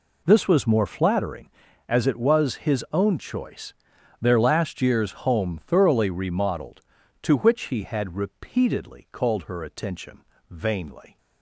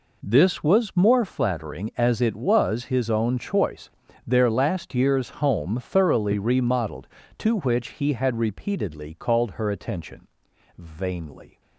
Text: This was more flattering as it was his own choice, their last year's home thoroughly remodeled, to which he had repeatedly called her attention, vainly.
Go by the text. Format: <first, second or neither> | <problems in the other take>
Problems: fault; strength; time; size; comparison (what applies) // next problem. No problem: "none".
neither | none